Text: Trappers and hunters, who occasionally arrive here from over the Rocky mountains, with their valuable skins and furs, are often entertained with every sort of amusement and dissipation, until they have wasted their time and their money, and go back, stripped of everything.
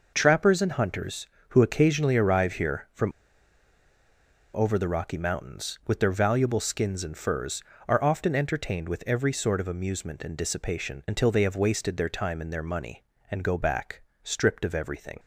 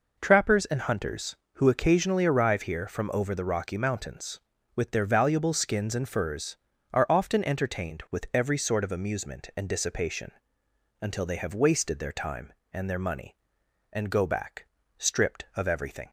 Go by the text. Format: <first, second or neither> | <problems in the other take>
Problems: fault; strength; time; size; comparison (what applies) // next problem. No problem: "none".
second | pauses between "from" and "over"; strong; at 3.1 s; 1.4 s long